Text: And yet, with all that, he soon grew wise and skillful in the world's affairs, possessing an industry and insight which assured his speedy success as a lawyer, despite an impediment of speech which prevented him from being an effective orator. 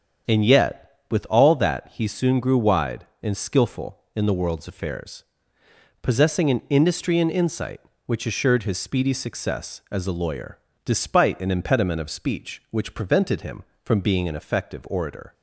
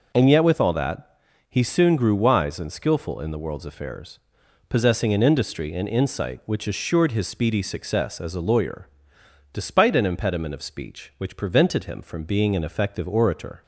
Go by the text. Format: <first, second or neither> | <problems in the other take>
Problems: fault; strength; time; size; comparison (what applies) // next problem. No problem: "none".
second | starts louder than the rest; until 1.4 s; 6.5 dB // says "wide" for "wise"; at 2.5 s